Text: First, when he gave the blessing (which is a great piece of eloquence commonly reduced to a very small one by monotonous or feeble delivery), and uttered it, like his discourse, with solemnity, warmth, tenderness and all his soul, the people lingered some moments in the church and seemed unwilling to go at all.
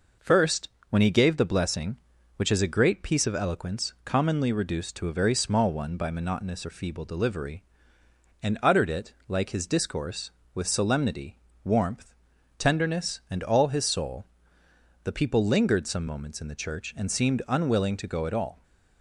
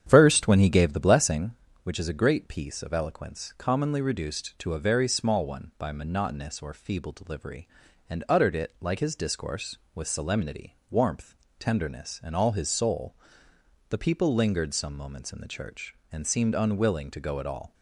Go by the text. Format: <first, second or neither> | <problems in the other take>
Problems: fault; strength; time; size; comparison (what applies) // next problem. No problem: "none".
first | starts louder than the rest; strong; until 1.6 s; 9 dB